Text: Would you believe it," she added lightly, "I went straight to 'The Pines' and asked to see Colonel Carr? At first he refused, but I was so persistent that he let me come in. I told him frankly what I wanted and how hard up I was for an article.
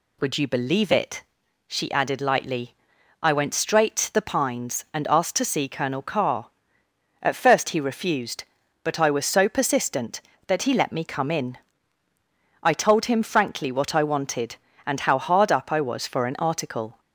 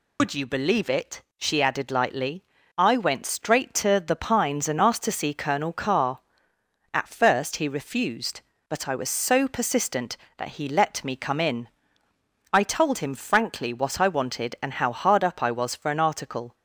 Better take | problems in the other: first | loses the start of "Would"; at 0.1 s; 130 ms

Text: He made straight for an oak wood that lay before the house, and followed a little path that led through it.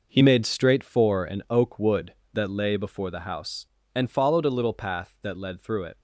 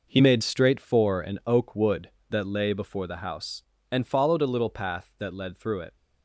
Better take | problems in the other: neither | none

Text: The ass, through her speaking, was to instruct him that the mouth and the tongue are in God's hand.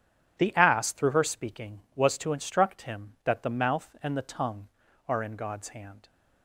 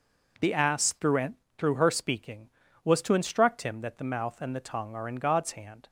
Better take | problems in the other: first | says "through" twice; at 1.5 s

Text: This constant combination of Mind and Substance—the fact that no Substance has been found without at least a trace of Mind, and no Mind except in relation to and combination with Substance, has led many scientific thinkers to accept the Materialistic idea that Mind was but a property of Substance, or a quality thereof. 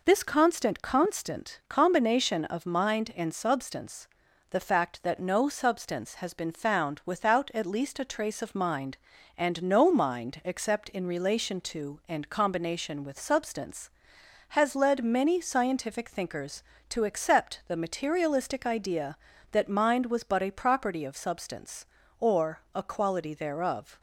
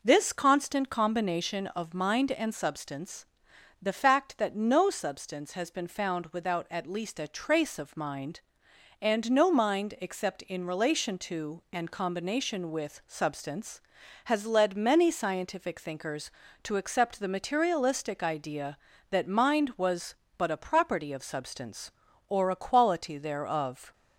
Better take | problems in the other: second | says "constant" twice; at 0.8 s

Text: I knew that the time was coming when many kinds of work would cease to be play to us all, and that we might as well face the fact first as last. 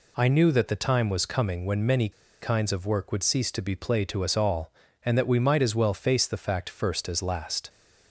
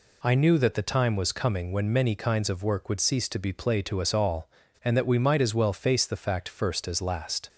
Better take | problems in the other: second | pauses between "many" and "kinds"; slight; at 2.0 s; 0.32 s long

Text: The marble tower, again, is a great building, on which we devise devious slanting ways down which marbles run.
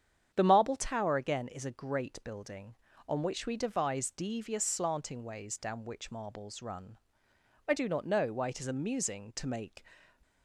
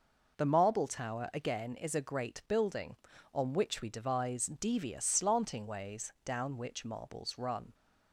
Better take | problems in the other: second | starts louder than the rest; strong; until 1.3 s; 8.5 dB // goes on to say "I do not know why it is amusing to make"; strong; from 7.6 s on; 2.1 s long

